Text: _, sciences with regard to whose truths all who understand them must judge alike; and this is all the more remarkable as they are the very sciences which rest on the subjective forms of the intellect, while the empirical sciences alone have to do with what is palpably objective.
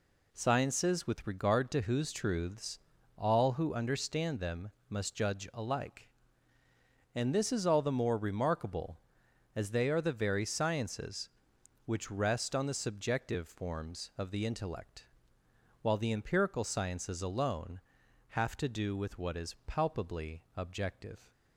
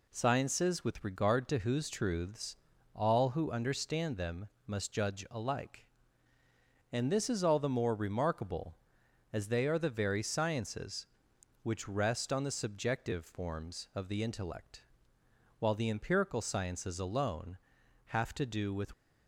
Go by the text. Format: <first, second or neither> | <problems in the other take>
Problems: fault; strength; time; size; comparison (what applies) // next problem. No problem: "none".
first | pauses between "truths" and "all"; at 2.5 s; 0.38 s long; also in the first // pauses between "them" and "must"; slight; at 4.4 s; 0.16 s long; slight in the first // stops before "what is palpably objective"; at 18.9 s